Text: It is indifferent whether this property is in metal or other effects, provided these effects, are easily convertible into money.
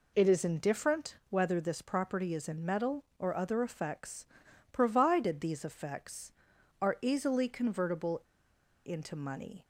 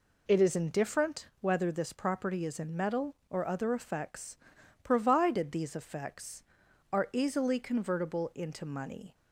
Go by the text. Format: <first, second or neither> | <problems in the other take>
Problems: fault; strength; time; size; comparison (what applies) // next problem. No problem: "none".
second | pauses between "convertible" and "into"; noticeable; at 8.1 s; 0.66 s long